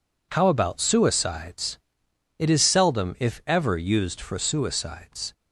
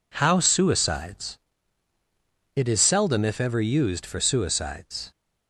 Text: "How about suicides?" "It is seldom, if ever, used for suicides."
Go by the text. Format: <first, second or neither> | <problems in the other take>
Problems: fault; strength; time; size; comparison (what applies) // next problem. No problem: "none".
first | skips "about"; at 0.4 s